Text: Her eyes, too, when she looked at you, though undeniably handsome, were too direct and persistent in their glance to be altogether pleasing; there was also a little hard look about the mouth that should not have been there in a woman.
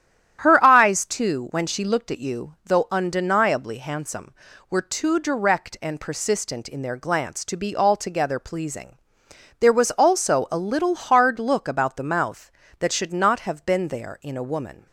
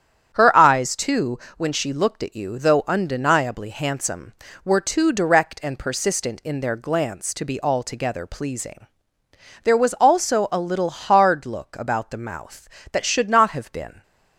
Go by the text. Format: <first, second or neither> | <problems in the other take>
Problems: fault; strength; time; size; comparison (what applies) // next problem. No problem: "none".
first | starts louder than the rest; strong; until 1.3 s; 9.5 dB; strong in the first // stops before "there in a woman"; at 14.0 s